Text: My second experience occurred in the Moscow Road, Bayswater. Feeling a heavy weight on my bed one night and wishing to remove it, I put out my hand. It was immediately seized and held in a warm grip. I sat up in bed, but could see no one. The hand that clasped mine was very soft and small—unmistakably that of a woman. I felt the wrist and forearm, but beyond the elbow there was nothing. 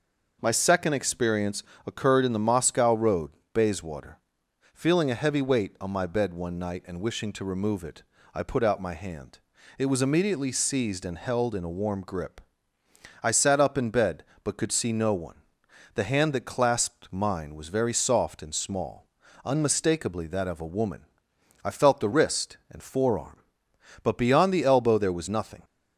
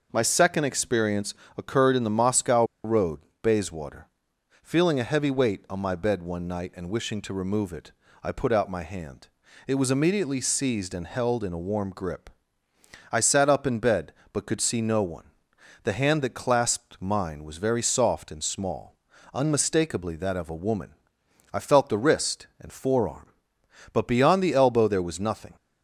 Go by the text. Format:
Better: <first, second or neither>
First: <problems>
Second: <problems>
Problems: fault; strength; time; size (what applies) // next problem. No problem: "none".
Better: first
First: pauses between "experience" and "occurred"; slight; at 1.6 s; 0.24 s long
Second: pauses between "experience" and "occurred"; slight; at 1.3 s; 0.24 s long // pauses between "Moscow" and "Road"; slight; at 2.6 s; 0.20 s long